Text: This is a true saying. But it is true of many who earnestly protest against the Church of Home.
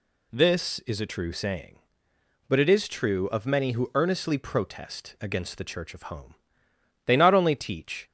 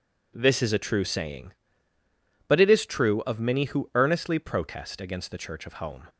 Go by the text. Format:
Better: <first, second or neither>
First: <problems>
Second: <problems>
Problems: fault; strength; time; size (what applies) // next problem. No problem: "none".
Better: second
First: goes on to say "They not only teach"; noticeable; from 7.0 s on; 1.0 s long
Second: none